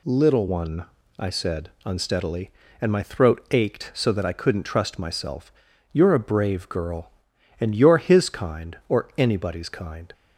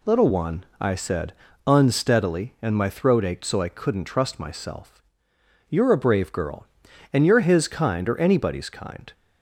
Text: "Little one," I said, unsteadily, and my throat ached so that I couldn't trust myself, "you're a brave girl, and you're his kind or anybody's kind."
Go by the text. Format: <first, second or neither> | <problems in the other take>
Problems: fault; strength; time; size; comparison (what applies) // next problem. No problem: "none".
first | skips "that"; at 3.6 s